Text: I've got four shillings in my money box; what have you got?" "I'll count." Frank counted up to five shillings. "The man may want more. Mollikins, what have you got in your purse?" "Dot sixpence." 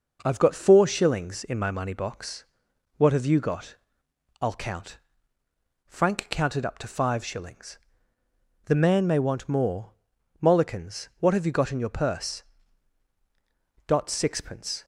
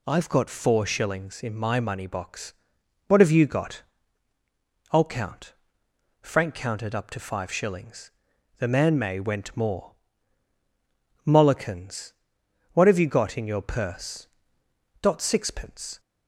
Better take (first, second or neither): first